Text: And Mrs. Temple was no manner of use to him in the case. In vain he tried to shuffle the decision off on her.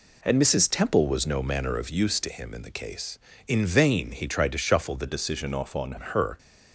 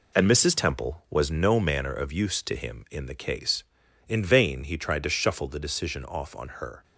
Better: second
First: changes voice from "decision" to "on"; from 5.0 to 5.9 s; 0.9 s long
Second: none

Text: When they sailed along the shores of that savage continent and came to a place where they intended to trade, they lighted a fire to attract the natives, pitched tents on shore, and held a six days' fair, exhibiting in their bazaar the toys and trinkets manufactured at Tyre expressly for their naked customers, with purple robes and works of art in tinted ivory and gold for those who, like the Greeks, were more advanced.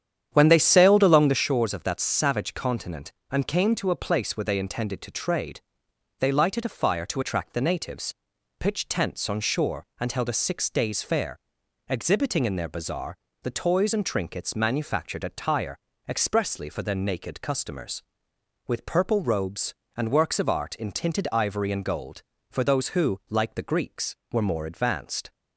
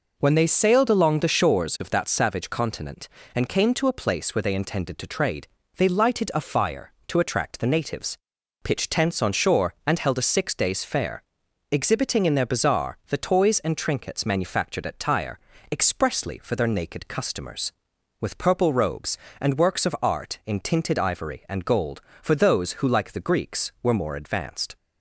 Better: second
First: starts louder than the rest; strong; until 1.4 s; 9 dB // pauses between "bazaar" and "the"; slight; at 13.1 s; 0.28 s long // pauses between "Tyre" and "expressly"; slight; at 15.7 s; 0.30 s long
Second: pauses between "Tyre" and "expressly"; slight; at 15.3 s; 0.32 s long

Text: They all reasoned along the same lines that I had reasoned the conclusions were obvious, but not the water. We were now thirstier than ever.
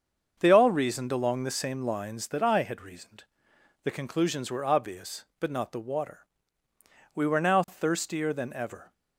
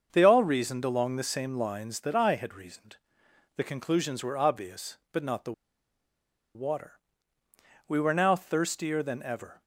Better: first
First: starts louder than the rest; until 1.4 s; 6.5 dB // pauses between "reasoned" and "the"; noticeable; at 3.2 s; 0.60 s long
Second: starts louder than the rest; until 1.1 s; 6.5 dB // pauses between "reasoned" and "the"; noticeable; at 2.9 s; 0.60 s long // pauses between "the" and "water"; at 5.5 s; 1.0 s long

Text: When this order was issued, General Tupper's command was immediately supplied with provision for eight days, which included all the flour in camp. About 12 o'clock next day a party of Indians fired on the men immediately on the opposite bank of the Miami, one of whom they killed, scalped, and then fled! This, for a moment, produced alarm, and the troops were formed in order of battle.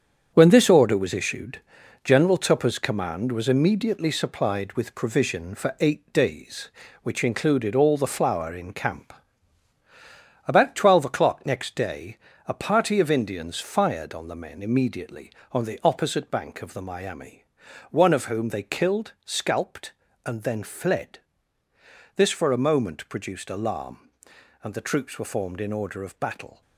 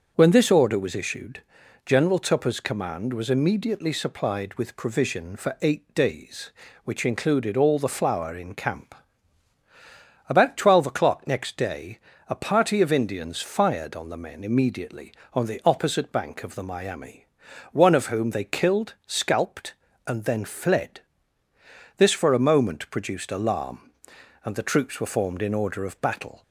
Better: second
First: gets quieter; strong; throughout; 8.5 dB // starts louder than the rest; strong; until 1.3 s; 8 dB // pauses between "day" and "a"; slight; at 12.1 s; 0.30 s long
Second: starts louder than the rest; until 1.1 s; 6.5 dB // pauses between "day" and "a"; slight; at 11.9 s; 0.30 s long

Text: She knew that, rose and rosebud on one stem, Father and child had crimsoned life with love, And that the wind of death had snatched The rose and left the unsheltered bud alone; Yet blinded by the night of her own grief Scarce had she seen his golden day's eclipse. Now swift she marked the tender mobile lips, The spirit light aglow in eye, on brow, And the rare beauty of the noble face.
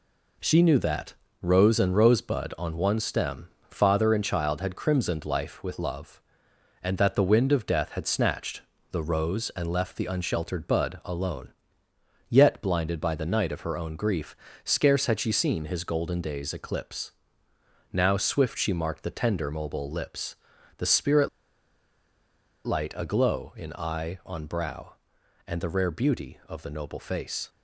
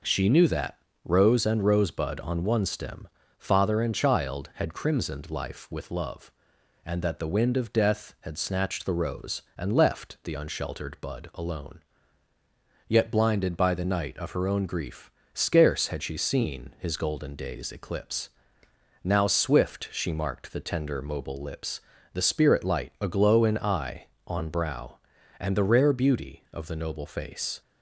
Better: second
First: pauses between "snatched" and "The"; slight; at 8.6 s; 0.30 s long // pauses between "grief" and "Scarce"; slight; at 14.3 s; 0.26 s long // pauses between "spirit" and "light"; strong; at 21.2 s; 1.3 s long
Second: pauses between "grief" and "Scarce"; slight; at 15.1 s; 0.24 s long

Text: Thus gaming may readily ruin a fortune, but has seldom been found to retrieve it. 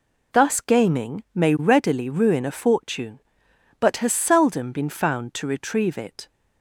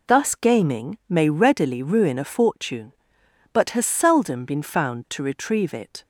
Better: neither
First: none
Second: none

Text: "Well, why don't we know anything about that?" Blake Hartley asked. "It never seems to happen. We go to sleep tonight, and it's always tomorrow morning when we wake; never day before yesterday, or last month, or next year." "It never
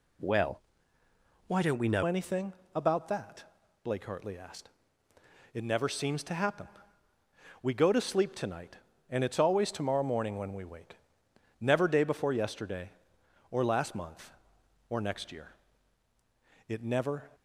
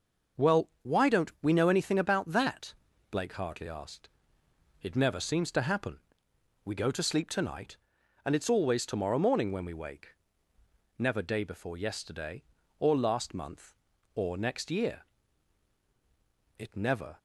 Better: second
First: changes voice at "anything"; from 2.0 s on; 15.3 s long // pauses between "anything" and "about"; slight; at 2.5 s; 0.22 s long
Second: none

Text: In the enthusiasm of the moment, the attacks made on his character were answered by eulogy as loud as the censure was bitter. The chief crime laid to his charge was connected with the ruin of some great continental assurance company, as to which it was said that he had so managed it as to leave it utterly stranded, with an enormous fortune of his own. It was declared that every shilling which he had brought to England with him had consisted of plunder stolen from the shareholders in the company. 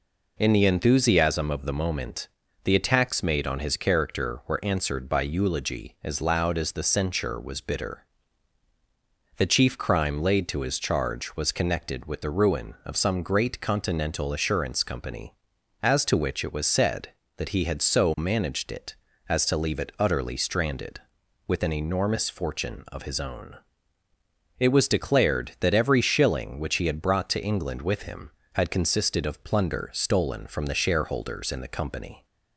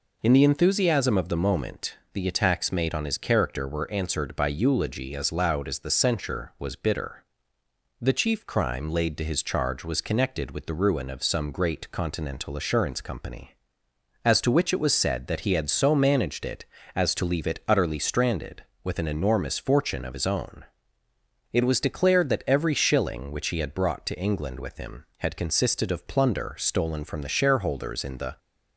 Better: first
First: none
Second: stops before "company"; at 28.3 s

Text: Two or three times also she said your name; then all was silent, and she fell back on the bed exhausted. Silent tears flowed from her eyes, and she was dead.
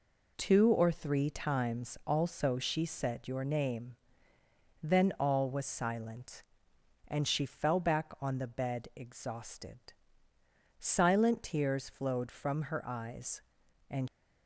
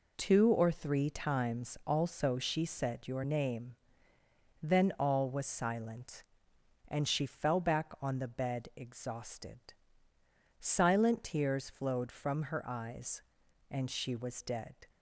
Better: second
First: stops before "she was dead"; at 14.0 s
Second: none

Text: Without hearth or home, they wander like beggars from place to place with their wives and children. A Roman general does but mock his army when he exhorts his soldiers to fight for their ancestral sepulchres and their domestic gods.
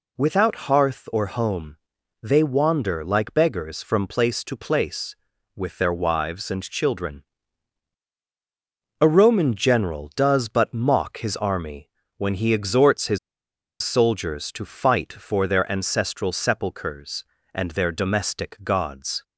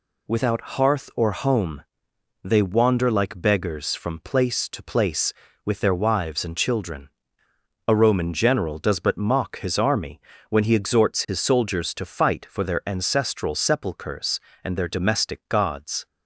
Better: second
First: pauses between "army" and "when"; slight; at 11.8 s; 0.26 s long // pauses between "his" and "soldiers"; noticeable; at 13.1 s; 0.64 s long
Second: pauses between "army" and "when"; slight; at 10.2 s; 0.30 s long

